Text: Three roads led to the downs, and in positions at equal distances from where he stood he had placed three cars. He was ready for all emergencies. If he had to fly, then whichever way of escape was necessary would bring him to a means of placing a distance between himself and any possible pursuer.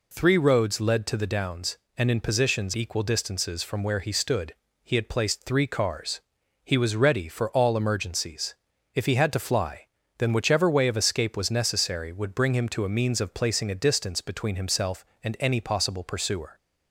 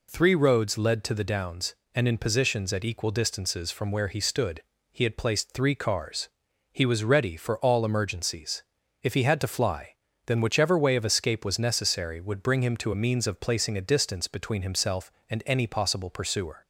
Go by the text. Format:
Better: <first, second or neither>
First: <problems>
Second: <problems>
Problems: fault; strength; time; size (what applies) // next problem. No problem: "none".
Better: second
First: skips "at"; at 2.7 s // pauses between "stood" and "he"; slight; at 4.5 s; 0.30 s long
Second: pauses between "stood" and "he"; slight; at 4.6 s; 0.30 s long